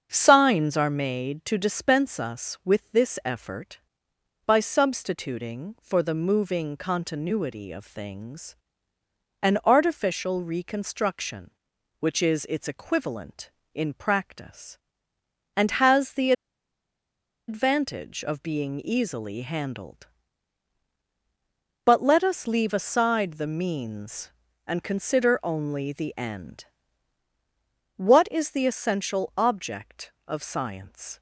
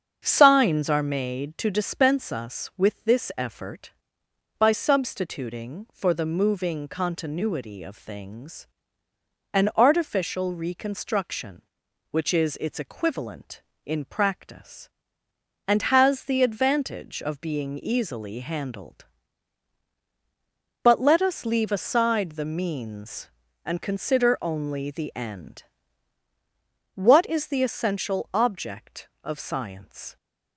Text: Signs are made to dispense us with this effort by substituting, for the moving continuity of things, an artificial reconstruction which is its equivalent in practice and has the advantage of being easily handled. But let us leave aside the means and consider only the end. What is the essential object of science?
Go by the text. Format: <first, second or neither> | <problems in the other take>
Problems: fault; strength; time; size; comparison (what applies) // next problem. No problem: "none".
second | starts louder than the rest; until 1.1 s; 7 dB; also in the second // pauses between "the" and "advantage"; at 16.3 s; 1.1 s long